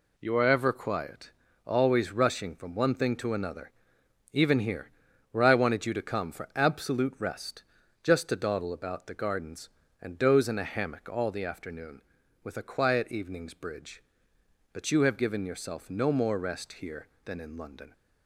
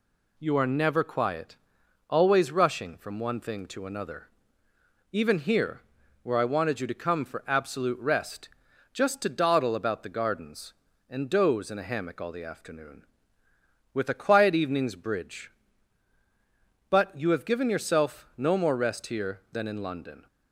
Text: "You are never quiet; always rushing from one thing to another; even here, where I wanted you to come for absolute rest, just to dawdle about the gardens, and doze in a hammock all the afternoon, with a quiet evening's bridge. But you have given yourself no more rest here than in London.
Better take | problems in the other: second | says "ever" for "never"; at 0.4 s

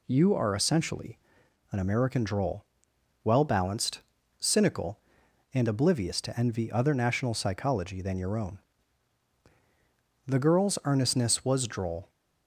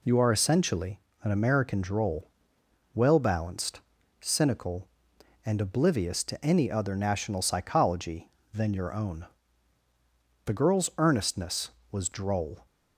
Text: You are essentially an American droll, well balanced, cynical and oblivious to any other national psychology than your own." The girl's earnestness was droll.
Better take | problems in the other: second | pauses between "essentially" and "an"; noticeable; at 1.1 s; 0.54 s long; slight in the second // says "envy" for "any"; at 6.3 s

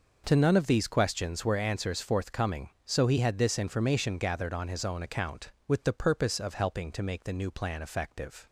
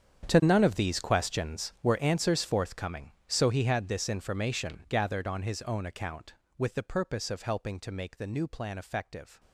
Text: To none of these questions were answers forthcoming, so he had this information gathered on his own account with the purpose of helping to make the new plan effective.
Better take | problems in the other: first | gets quieter; strong; throughout; 18 dB

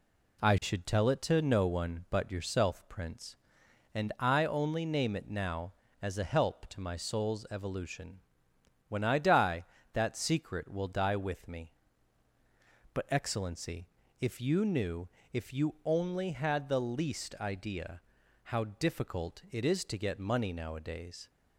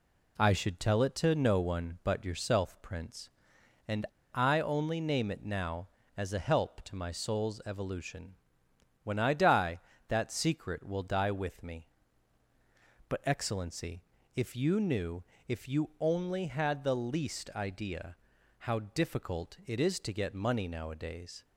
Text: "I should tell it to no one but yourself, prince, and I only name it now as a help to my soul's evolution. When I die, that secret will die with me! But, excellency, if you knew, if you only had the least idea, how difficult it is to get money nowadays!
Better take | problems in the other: first | pauses between "and" and "I"; slight; at 4.0 s; 0.29 s long

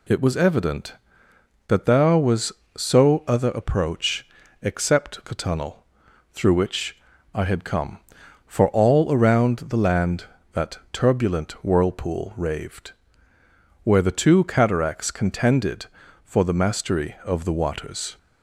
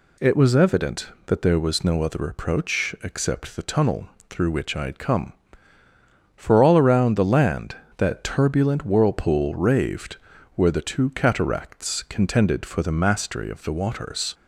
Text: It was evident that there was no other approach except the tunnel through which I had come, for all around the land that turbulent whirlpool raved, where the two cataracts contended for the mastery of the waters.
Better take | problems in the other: second | says "so" for "no"; at 2.7 s // pauses between "approach" and "except"; slight; at 4.2 s; 0.36 s long // pauses between "tunnel" and "through"; noticeable; at 5.8 s; 0.48 s long; slight in the second // pauses between "which" and "I"; at 6.9 s; 0.38 s long // pauses between "that" and "turbulent"; slight; at 10.7 s; 0.16 s long

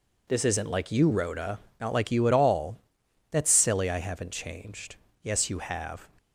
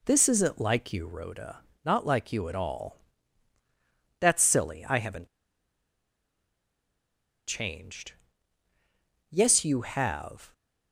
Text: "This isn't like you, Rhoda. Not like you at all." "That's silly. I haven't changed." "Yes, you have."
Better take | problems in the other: first | pauses between "haven't" and "changed"; strong; at 5.2 s; 2.2 s long

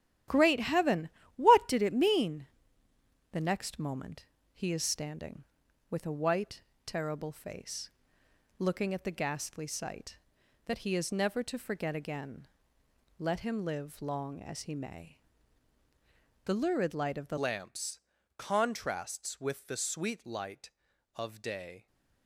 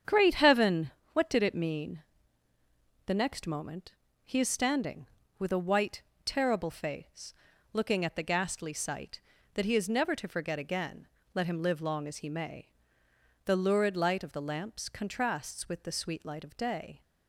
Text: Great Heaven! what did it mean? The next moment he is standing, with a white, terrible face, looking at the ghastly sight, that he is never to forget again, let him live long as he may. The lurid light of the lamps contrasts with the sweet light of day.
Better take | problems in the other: second | starts louder than the rest; strong; until 1.5 s; 12 dB; strong in the second // pauses between "moment" and "he"; slight; at 4.2 s; 0.26 s long; slight in the second // changes voice at "lamps"; from 17.3 s on; 4.5 s long // pauses between "lamps" and "contrasts"; slight; at 18.0 s; 0.36 s long

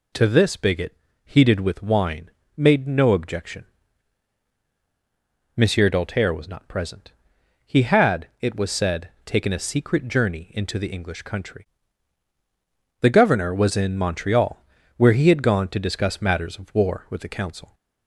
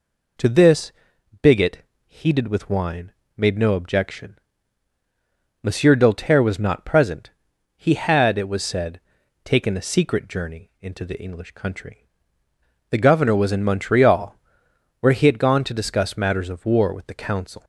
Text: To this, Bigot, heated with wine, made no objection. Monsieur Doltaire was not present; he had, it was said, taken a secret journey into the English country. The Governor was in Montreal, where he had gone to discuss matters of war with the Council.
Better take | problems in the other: neither | none

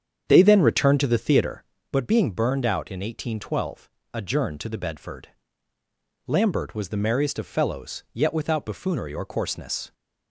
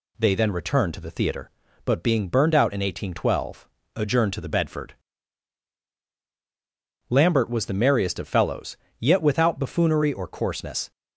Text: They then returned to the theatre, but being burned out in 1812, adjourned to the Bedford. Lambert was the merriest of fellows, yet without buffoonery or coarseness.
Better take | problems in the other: second | starts louder than the rest; strong; until 1.8 s; 8 dB

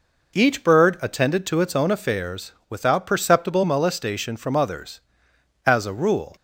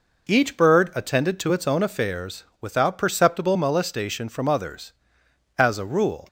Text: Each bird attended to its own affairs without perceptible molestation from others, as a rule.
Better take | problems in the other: neither | pauses between "affairs" and "without"; slight; the same in both

